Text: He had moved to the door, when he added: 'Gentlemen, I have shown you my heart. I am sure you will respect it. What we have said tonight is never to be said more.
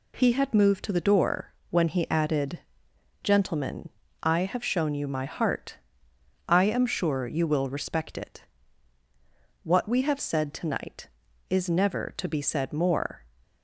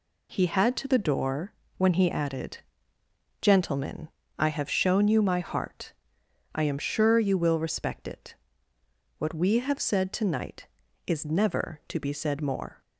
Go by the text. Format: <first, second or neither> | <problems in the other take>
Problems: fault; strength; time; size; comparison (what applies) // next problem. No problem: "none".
first | skips "moved"; at 0.7 s